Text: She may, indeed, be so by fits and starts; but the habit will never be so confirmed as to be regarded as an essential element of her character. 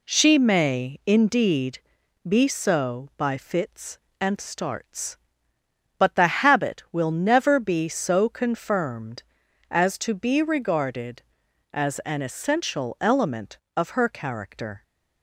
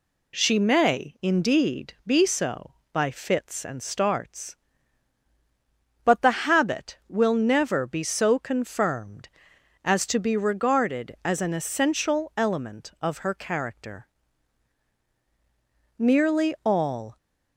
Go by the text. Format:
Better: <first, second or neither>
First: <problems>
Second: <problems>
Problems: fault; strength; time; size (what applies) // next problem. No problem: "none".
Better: first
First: none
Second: goes on to say "Nearly all"; noticeable; from 16.0 s on; 1.1 s long